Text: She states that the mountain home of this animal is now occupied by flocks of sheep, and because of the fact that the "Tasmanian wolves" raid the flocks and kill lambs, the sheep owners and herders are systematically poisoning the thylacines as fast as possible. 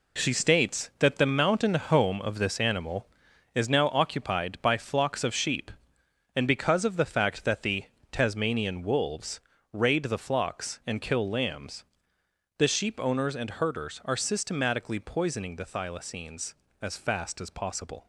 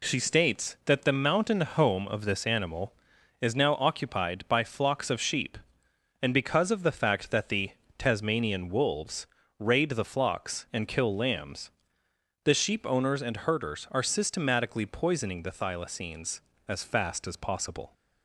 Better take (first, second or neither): second